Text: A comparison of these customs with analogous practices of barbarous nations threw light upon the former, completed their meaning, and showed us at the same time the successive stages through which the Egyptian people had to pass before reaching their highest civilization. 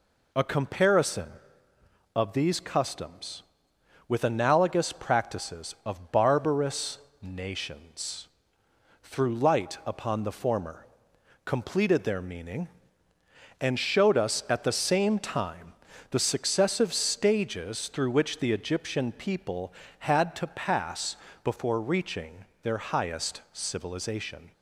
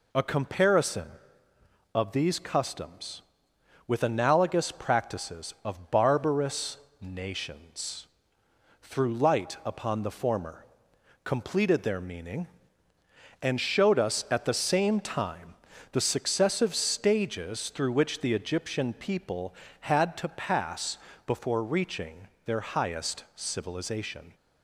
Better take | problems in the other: neither | pauses between "barbarous" and "nations"; slight; the same in both // pauses between "nations" and "threw"; noticeable; the same in both // pauses between "time" and "the"; the same in both // pauses between "pass" and "before"; slight; the same in both // pauses between "reaching" and "their"; slight; the same in both

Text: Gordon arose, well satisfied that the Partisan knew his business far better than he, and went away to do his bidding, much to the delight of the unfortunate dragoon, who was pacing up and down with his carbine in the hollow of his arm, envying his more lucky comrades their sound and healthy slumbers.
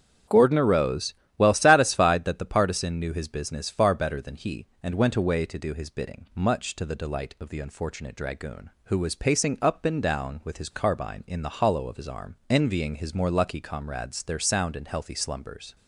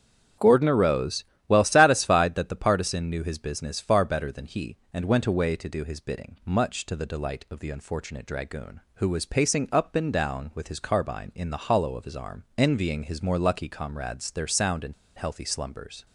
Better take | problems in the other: first | starts louder than the rest; strong; until 1.6 s; 8.5 dB; strong in the first // pauses between "and" and "healthy"; slight; at 14.9 s; 0.23 s long

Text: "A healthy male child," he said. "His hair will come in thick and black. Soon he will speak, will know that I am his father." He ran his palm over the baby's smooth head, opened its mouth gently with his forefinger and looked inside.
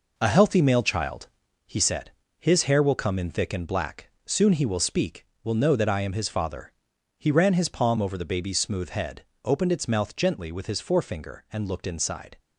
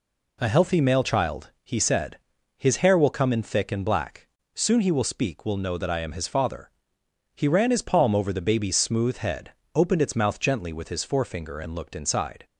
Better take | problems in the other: second | gets quieter; strong; throughout; 7.5 dB

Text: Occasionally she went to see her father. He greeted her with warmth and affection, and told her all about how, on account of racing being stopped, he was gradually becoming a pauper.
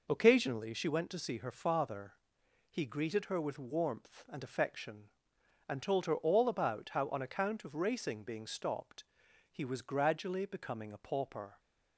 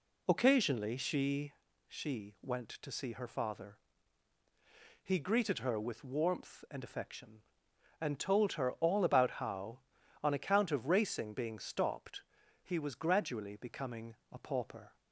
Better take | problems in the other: first | says "she" twice; at 1.8 s // pauses between "becoming" and "a"; slight; at 14.1 s; 0.16 s long

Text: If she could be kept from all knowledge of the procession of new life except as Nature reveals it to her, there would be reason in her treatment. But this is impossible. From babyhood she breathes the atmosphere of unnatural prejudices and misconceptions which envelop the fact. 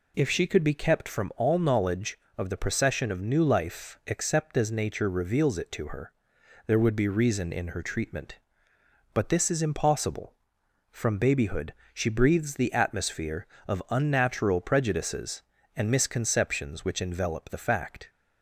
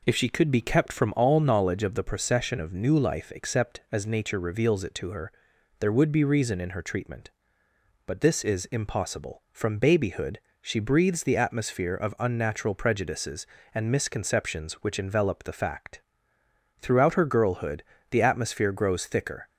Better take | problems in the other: first | pauses between "babyhood" and "she"; slight; at 10.3 s; 0.20 s long; slight in the first // goes on to say "Throughout her girlhood the atmosphere grows thicker"; strong; from 16.7 s on; 2.6 s long

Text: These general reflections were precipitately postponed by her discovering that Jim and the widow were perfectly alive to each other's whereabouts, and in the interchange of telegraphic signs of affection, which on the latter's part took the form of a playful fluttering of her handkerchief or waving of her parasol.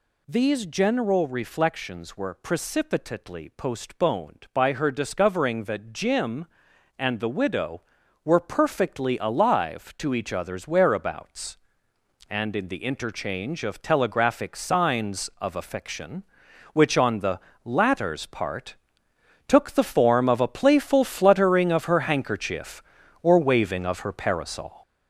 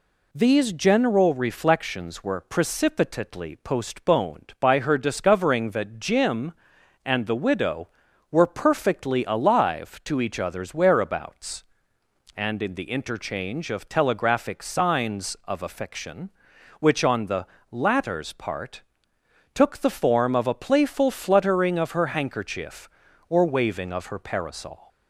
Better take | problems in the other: second | gets louder; noticeable; throughout; 6 dB // pauses between "the" and "latter's"; slight; at 17.3 s; 0.24 s long; slight in the second // pauses between "part" and "took"; noticeable; at 18.7 s; 0.70 s long; noticeable in the second

